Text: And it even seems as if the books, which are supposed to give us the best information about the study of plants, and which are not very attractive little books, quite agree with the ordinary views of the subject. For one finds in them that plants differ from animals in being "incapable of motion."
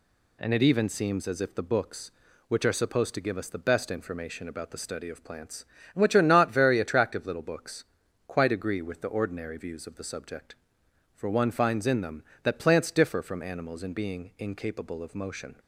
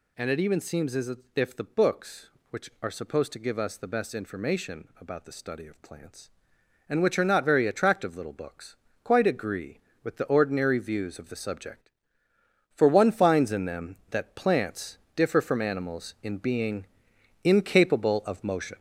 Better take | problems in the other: first | gets louder; noticeable; throughout; 4.5 dB // pauses between "as" and "if"; slight; at 1.1 s; 0.20 s long // pauses between "plants" and "differ"; slight; at 14.9 s; 0.18 s long // pauses between "being" and "incapable"; noticeable; at 16.8 s; 0.56 s long

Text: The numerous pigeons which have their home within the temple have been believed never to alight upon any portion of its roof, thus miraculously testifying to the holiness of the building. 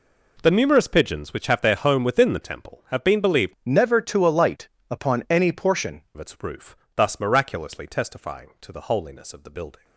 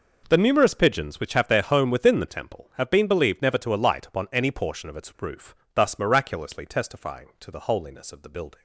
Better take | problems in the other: second | changes voice from "never" to "portion"; from 3.6 to 6.0 s; 2.4 s long // pauses between "alight" and "upon"; slight; at 4.6 s; 0.22 s long

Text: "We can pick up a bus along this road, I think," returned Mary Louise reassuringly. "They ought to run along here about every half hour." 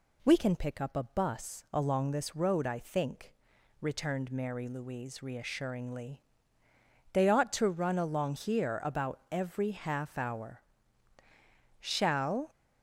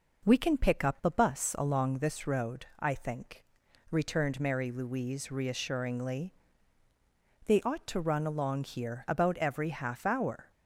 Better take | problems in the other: second | goes on to say "Shall"; noticeable; from 11.7 s on; 0.70 s long

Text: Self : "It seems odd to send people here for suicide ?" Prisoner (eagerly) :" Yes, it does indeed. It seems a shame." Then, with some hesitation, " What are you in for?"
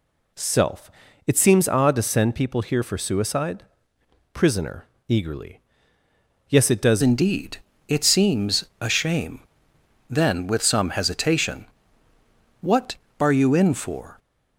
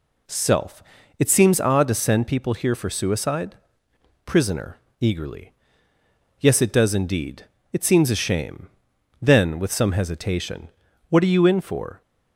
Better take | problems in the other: second | changes voice at "indeed"; from 7.0 s on; 7.1 s long // pauses between "seems" and "a"; slight; at 8.6 s; 0.16 s long

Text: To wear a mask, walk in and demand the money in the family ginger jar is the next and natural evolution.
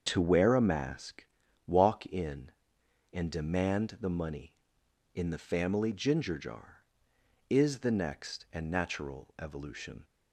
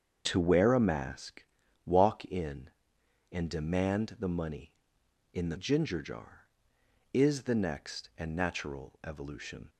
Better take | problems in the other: first | starts louder than the rest; until 1.3 s; 7 dB; also in the first // skips "family"; at 5.5 s

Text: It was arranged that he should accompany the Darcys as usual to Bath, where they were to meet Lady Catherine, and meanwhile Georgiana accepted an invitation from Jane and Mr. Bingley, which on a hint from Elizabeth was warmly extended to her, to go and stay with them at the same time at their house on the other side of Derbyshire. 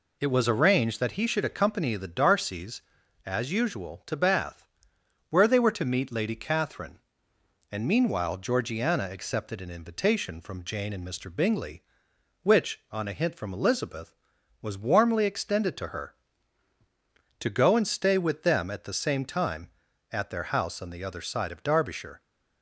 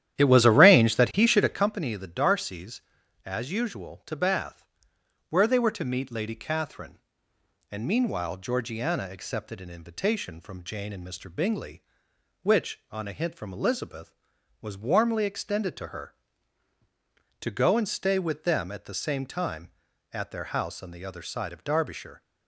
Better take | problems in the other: first | starts louder than the rest; strong; until 1.7 s; 11 dB

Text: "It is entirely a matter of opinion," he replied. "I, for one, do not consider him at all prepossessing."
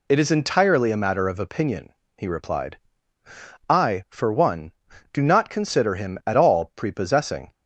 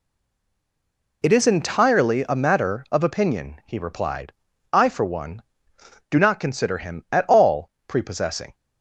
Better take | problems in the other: first | stays silent before the first word; noticeable; until 1.2 s; 1.2 s long // pauses between "all" and "prepossessing"; slight; at 7.6 s; 0.20 s long

